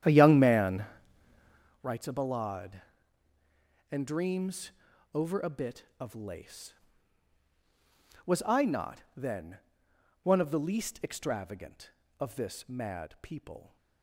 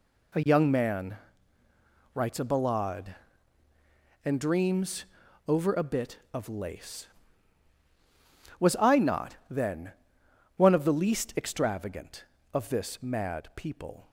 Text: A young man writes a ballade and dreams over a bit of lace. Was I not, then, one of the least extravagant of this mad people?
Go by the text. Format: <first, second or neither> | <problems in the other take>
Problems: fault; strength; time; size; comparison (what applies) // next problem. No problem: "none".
second | starts louder than the rest; strong; until 1.8 s; 10.5 dB // pauses between "man" and "writes"; noticeable; at 0.8 s; 0.98 s long; noticeable in the second // pauses between "dreams" and "over"; at 4.7 s; 0.42 s long; also in the second